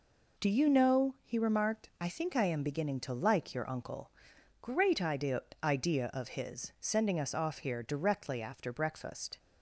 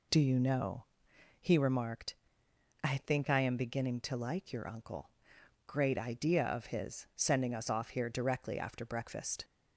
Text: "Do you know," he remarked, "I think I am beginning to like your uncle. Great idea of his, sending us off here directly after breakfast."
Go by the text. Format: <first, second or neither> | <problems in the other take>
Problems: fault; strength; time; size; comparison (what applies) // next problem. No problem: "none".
second | says "idea" twice; at 5.6 s